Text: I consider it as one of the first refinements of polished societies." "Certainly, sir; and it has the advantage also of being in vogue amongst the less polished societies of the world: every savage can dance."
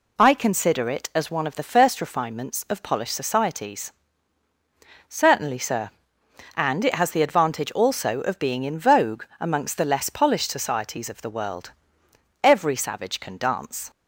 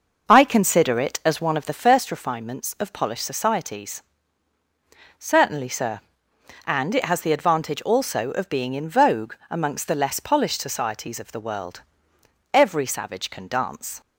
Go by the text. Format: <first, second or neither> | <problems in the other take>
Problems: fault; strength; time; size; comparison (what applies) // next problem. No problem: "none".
first | starts louder than the rest; noticeable; until 2.0 s; 5.5 dB // pauses between "vogue" and "amongst"; slight; at 9.3 s; 0.16 s long; slight in the first